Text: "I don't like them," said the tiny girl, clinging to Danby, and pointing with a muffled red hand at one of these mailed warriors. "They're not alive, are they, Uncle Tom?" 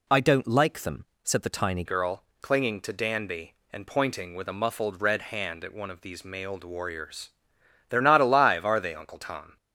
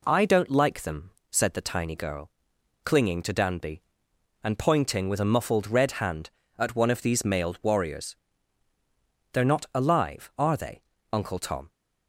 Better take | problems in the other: second | changes voice at "girl"; from 1.8 s on; 7.7 s long

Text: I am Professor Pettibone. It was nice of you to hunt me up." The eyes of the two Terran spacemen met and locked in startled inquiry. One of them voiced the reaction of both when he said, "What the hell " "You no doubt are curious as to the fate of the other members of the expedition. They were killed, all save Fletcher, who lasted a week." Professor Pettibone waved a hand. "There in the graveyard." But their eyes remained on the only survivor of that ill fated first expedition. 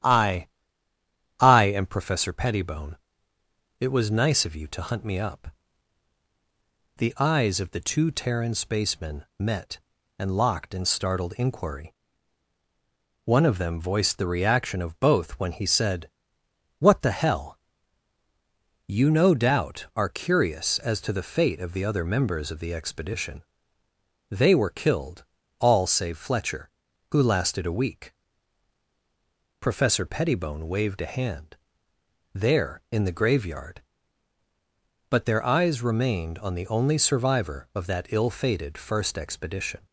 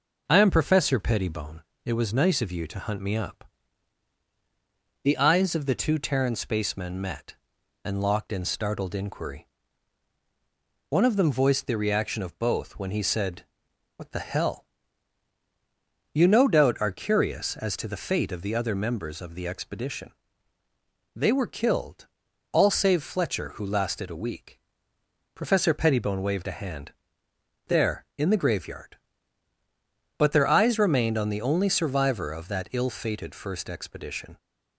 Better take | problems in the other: second | starts louder than the rest; strong; until 1.9 s; 11 dB // says "I" twice; at 1.3 s

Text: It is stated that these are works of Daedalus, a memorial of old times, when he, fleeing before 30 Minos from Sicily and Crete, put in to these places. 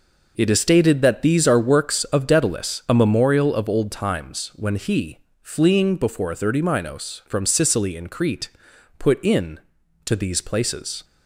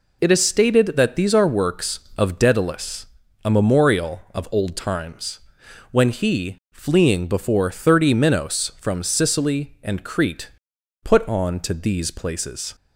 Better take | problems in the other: first | says "on" for "in"; at 11.2 s

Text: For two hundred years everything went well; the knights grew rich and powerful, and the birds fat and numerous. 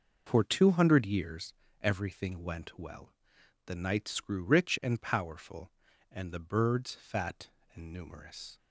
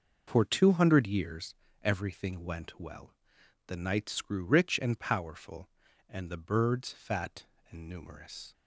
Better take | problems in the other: neither | pauses between "years" and "everything"; slight; the same in both

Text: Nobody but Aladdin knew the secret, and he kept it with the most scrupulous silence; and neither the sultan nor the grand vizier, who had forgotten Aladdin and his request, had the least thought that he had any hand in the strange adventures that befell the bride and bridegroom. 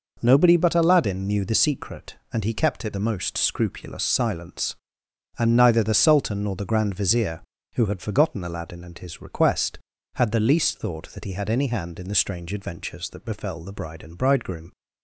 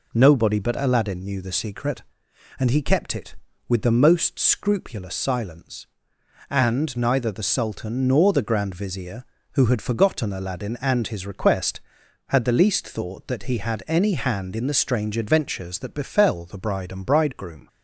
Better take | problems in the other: second | skips "with"; at 2.9 s

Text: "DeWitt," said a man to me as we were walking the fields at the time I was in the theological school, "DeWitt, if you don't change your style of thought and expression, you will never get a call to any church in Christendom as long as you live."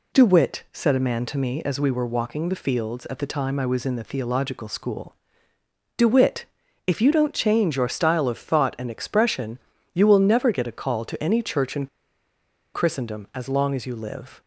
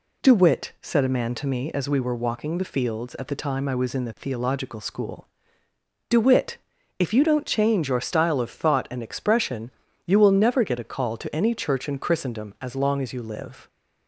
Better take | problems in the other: second | pauses between "in" and "Christendom"; noticeable; at 11.8 s; 0.88 s long

